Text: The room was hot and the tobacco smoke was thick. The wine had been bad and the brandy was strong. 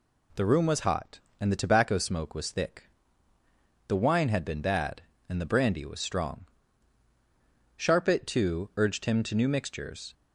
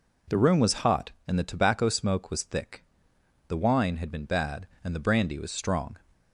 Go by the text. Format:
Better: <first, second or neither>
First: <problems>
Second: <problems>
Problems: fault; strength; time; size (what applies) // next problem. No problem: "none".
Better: second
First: goes on to say "Sharpit too urged him to new mixtures"; strong; from 7.7 s on; 2.3 s long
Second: none